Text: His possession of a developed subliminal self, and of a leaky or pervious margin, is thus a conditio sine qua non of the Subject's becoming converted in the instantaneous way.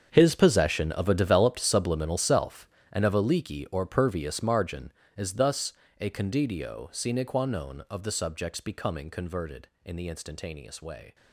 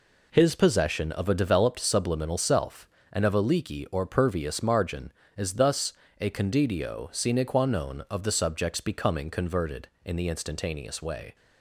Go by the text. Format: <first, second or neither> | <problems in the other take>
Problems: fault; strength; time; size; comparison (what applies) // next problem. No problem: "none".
second | gets quieter; strong; throughout; 15 dB // pauses between "thus" and "a"; slight; at 5.7 s; 0.30 s long; slight in the second